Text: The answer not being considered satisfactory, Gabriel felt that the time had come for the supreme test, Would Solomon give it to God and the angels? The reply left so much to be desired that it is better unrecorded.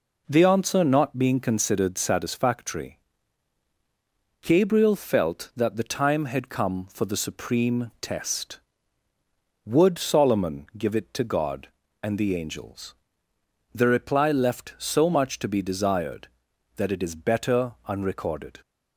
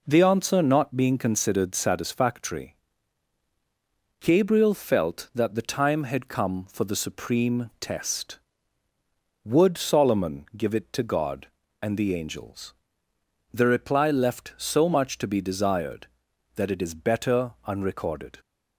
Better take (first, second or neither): neither